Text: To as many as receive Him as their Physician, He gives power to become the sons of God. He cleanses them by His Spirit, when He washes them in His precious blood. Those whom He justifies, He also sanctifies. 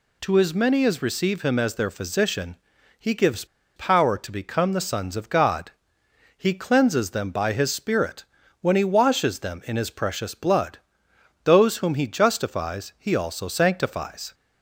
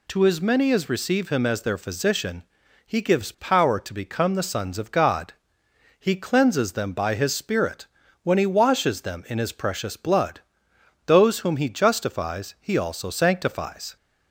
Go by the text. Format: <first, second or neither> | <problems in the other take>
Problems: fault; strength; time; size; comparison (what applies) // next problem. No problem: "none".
second | pauses between "gives" and "power"; slight; at 3.4 s; 0.30 s long